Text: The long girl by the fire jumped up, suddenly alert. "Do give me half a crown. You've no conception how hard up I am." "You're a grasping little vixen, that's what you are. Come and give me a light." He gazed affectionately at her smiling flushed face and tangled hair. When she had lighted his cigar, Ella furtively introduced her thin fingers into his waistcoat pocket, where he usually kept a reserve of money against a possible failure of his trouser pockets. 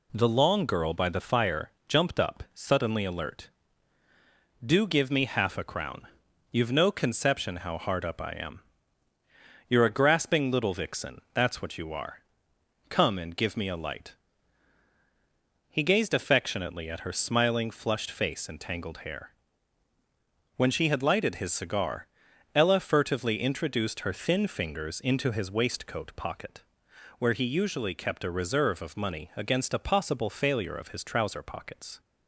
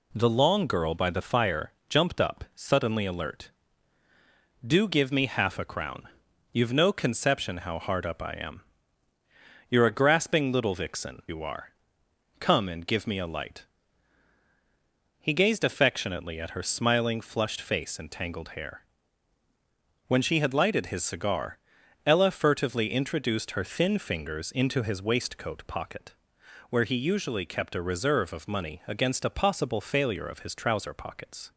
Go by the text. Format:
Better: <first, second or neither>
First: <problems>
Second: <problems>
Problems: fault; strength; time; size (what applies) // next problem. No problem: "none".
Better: first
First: pauses between "fire" and "jumped"; slight; at 1.7 s; 0.16 s long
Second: pauses between "fire" and "jumped"; slight; at 1.7 s; 0.16 s long // skips "that's what"; at 11.2 s